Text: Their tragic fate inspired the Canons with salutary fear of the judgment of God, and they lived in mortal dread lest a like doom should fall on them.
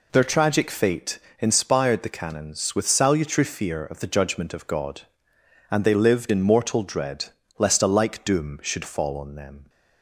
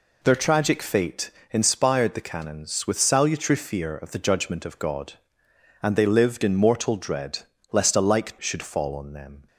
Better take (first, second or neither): first